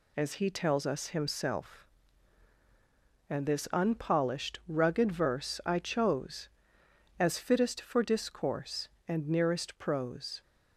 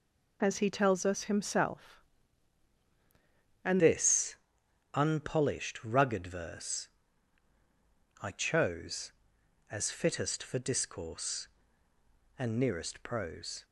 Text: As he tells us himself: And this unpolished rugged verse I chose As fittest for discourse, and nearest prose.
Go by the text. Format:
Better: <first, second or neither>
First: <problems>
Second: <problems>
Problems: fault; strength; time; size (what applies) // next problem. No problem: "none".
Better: first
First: none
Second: changes voice at "this"; from 3.7 s on; 9.9 s long // pauses between "this" and "unpolished"; noticeable; at 4.3 s; 0.58 s long // pauses between "verse" and "I"; strong; at 6.8 s; 1.3 s long